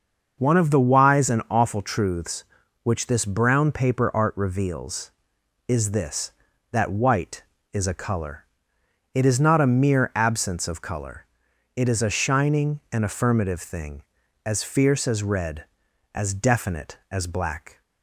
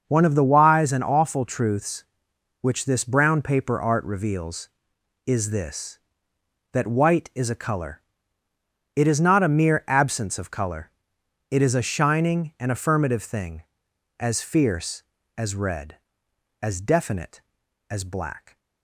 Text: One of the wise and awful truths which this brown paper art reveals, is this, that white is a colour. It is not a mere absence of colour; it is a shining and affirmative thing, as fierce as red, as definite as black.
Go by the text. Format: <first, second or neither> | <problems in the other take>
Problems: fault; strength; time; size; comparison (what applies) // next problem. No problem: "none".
neither | starts louder than the rest; the same in both